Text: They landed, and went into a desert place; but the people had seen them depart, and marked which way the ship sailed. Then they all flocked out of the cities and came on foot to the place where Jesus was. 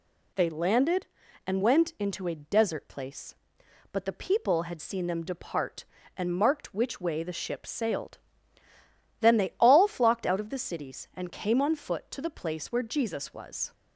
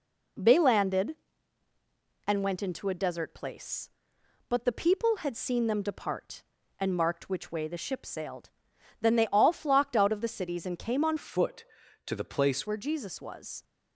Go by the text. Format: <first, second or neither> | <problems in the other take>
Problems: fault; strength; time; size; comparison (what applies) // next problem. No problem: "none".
first | changes voice from "foot" to "place"; from 11.1 to 12.6 s; 1.5 s long